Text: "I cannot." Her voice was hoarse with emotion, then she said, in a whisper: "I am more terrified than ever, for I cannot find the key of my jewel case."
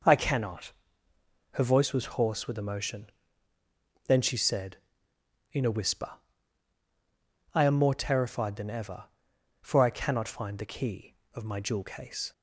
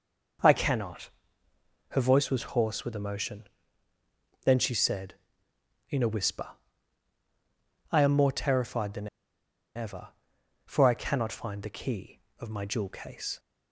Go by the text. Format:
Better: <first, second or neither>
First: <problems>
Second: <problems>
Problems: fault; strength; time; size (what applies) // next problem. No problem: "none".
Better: first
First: none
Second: pauses between "than" and "ever"; noticeable; at 9.0 s; 0.69 s long